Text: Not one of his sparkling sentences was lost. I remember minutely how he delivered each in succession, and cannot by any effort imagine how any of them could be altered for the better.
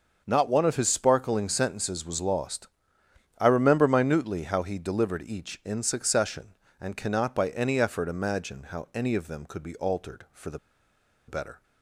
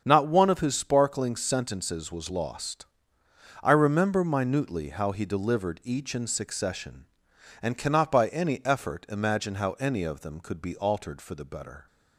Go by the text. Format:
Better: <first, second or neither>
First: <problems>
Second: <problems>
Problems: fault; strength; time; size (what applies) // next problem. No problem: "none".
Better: second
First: starts louder than the rest; until 1.2 s; 6.5 dB // pauses between "the" and "better"; noticeable; at 10.5 s; 0.69 s long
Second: starts louder than the rest; strong; until 1.0 s; 7.5 dB